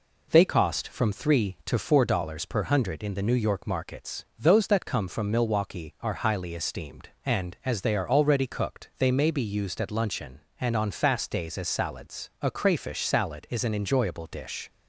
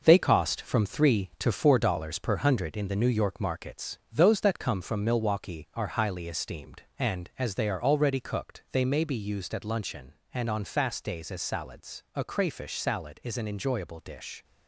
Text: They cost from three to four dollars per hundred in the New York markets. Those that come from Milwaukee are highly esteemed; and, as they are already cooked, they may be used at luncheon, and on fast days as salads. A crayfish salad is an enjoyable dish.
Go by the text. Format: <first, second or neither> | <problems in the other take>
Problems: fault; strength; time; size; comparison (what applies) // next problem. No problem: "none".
first | gets quieter; throughout; 6.5 dB